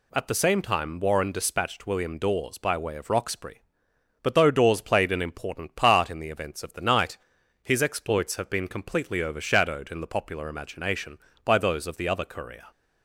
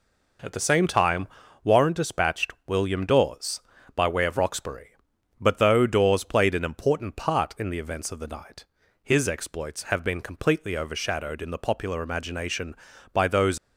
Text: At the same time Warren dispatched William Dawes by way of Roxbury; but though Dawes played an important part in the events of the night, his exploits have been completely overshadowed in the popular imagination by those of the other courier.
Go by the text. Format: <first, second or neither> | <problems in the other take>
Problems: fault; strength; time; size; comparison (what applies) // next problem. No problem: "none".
first | pauses between "time" and "Warren"; at 1.2 s; 0.38 s long // stops before "of the other courier"; at 13.5 s